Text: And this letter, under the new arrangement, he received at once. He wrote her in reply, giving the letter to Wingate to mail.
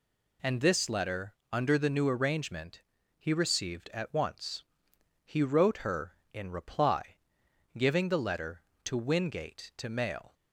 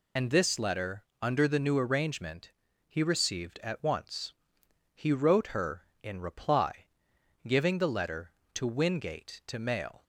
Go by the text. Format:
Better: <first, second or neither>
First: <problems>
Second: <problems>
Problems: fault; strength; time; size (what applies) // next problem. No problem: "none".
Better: first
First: none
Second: loses the start of "And"; at 0.1 s; 40 ms